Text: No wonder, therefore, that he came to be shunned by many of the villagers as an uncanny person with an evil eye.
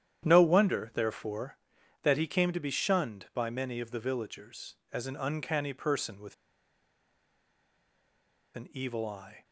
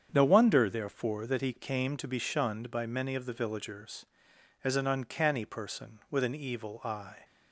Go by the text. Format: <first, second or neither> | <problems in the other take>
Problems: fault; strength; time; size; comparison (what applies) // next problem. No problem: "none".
second | starts louder than the rest; strong; until 1.3 s; 10 dB; strong in the second // pauses between "with" and "an"; strong; at 6.3 s; 2.2 s long